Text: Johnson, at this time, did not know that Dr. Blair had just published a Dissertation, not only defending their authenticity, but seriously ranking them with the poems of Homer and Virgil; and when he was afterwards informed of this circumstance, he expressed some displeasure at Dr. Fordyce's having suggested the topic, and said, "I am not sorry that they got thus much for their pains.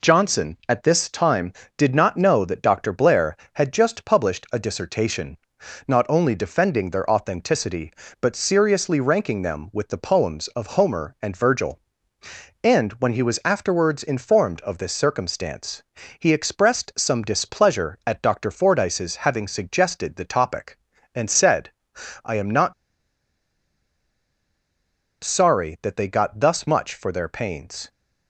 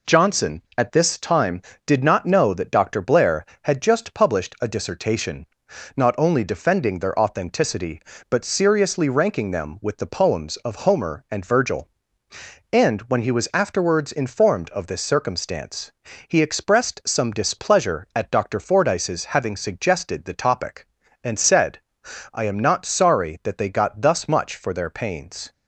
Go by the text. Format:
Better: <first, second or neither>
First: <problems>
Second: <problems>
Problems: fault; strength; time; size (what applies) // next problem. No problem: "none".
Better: second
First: pauses between "not" and "sorry"; strong; at 22.7 s; 2.4 s long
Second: none